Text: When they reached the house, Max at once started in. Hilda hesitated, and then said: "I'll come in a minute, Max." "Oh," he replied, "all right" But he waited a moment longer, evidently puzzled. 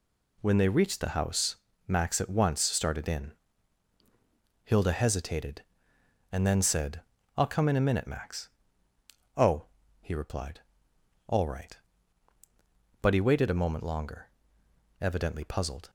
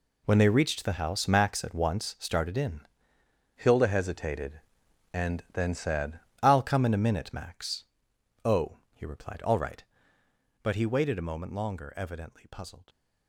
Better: first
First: none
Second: changes voice from "Hilda" to "said"; from 3.5 to 6.1 s; 2.6 s long

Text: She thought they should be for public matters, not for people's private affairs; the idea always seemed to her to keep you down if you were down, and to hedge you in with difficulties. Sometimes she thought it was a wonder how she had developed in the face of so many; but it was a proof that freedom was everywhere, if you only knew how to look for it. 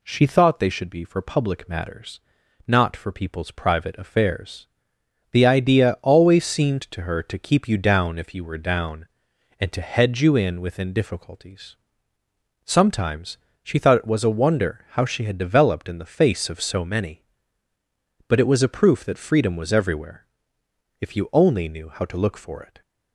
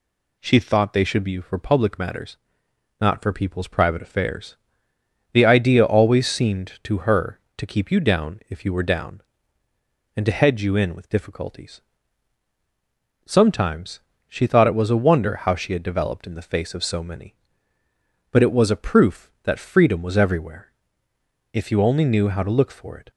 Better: second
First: says "within" for "with"; at 10.5 s // pauses between "Sometimes" and "she"; slight; at 13.3 s; 0.26 s long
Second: pauses between "Sometimes" and "she"; slight; at 13.9 s; 0.30 s long

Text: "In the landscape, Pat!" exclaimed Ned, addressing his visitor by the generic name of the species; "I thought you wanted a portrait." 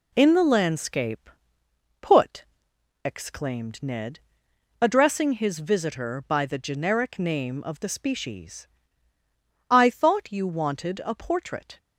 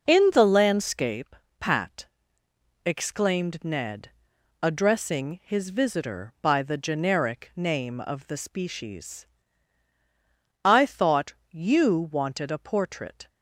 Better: second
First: says "Put" for "Pat"; at 2.0 s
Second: none

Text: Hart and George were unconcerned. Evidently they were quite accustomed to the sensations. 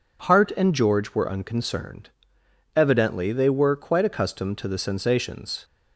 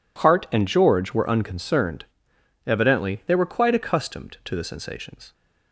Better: neither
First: none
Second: none

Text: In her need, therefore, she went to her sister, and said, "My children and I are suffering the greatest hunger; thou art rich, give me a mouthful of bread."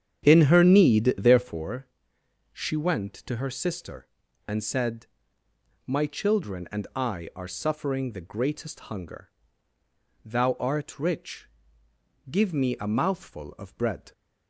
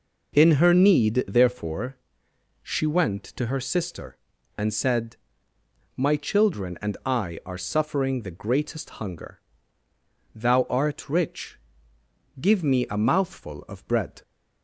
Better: second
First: starts louder than the rest; strong; until 1.6 s; 8.5 dB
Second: none

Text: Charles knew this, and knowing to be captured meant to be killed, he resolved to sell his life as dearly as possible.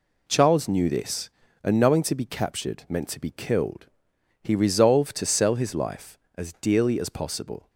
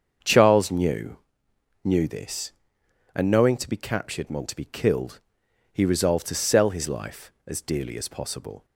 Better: first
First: none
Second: starts louder than the rest; until 1.8 s; 7 dB // says "knew" twice; at 1.8 s

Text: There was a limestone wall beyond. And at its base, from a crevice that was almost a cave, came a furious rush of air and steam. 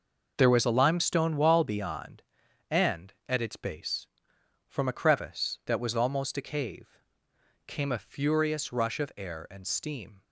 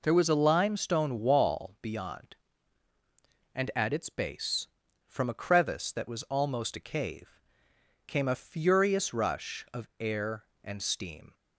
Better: neither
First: none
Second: none

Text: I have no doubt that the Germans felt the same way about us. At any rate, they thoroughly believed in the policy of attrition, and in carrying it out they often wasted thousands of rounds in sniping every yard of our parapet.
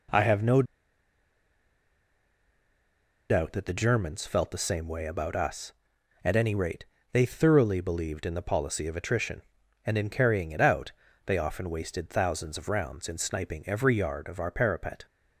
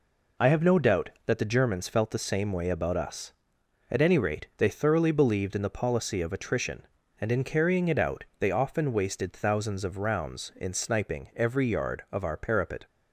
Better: second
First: pauses between "no" and "doubt"; strong; at 0.6 s; 2.6 s long // pauses between "out" and "they"; slight; at 10.9 s; 0.36 s long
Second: none

